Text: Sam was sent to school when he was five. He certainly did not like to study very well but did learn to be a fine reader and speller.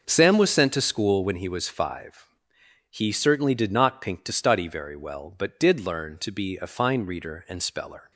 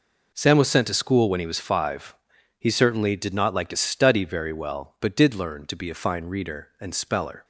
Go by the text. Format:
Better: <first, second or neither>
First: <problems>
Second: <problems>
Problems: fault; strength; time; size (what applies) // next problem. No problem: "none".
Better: second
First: says "pink" for "like"; at 4.0 s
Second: none